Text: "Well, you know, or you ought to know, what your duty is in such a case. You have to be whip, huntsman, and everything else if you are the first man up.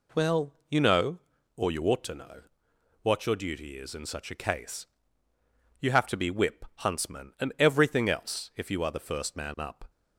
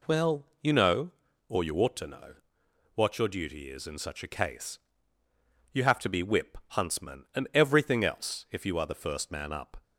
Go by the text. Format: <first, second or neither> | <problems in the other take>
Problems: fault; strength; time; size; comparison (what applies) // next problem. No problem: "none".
neither | none